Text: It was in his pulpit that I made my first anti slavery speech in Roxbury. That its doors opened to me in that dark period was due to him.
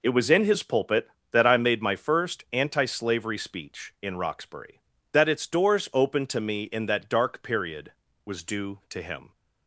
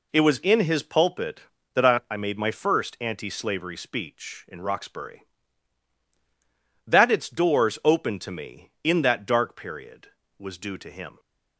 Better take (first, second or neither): first